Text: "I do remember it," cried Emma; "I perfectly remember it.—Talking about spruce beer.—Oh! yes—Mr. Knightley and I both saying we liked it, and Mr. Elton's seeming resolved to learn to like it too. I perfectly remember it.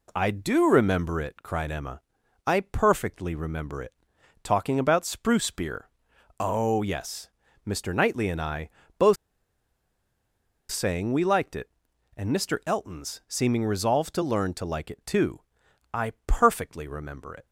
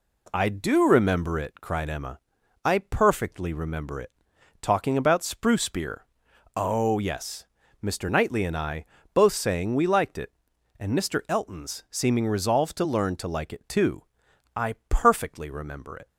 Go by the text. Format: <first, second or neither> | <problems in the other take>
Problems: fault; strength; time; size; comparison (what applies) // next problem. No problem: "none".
second | pauses between "I" and "both"; slight; at 8.7 s; 0.26 s long; slight in the second // pauses between "both" and "saying"; strong; at 9.1 s; 1.5 s long